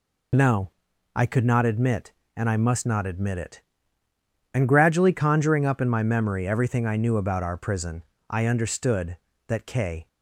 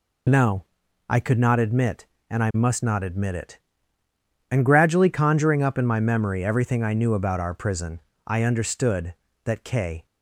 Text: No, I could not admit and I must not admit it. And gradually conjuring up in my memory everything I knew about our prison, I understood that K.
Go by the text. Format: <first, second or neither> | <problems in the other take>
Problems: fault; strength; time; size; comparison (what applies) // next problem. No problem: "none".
neither | none